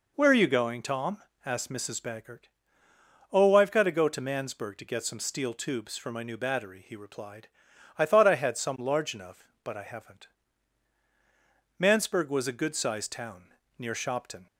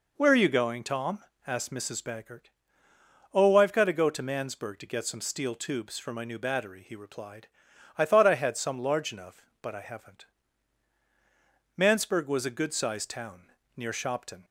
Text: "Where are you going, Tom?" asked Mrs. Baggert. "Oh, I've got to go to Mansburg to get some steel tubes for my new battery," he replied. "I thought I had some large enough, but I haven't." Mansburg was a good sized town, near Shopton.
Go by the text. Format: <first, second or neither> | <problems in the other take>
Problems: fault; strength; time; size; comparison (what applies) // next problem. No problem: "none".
neither | none